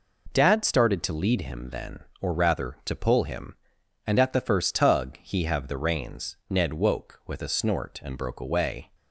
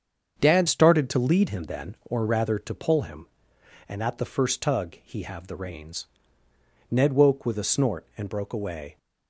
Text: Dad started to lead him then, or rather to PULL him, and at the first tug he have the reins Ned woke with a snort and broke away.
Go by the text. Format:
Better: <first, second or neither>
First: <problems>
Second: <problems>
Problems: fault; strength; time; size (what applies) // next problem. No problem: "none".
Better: first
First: none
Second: starts louder than the rest; strong; until 1.3 s; 7 dB // changes voice at "started"; from 0.6 s on; 8.3 s long // pauses between "reins" and "Ned"; noticeable; at 6.0 s; 0.86 s long